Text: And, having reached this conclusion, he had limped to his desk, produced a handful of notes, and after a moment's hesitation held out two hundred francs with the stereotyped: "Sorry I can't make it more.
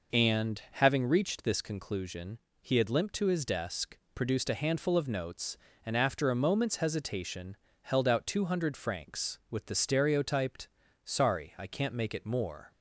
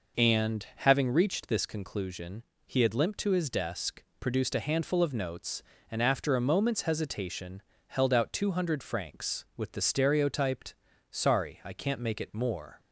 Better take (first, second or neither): neither